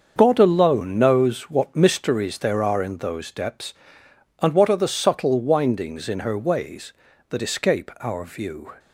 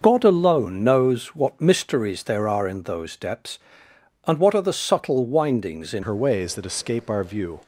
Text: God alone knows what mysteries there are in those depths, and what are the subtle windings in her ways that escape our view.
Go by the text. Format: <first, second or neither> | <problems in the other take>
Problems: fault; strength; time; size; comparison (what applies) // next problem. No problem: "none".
first | starts louder than the rest; noticeable; until 1.0 s; 6 dB; also in the first // changes voice at "her"; from 6.0 s on; 1.6 s long